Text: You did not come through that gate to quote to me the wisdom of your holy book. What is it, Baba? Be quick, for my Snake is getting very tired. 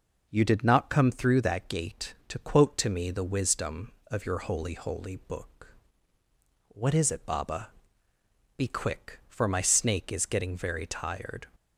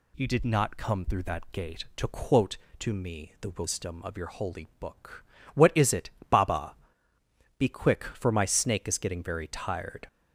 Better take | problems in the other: second | says "holy" twice; at 4.7 s

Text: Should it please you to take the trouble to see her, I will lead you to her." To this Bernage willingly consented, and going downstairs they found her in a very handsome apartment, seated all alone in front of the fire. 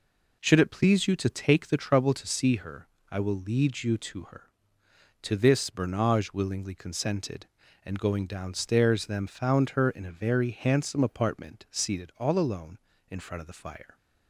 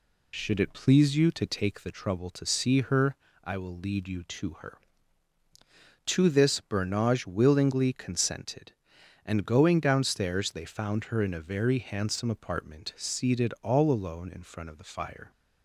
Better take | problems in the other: second | says "them" for "they"; at 9.0 s

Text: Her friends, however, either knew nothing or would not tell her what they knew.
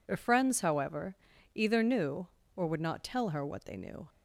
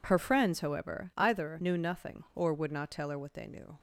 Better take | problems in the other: second | skips "nothing"; at 2.4 s

